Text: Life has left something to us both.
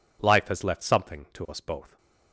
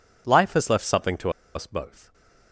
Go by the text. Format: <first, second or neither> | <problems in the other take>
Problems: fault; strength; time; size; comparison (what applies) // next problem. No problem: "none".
first | pauses between "to" and "us"; slight; at 1.2 s; 0.25 s long // stays silent after the last word; slight; from 2.0 s on; 0.5 s long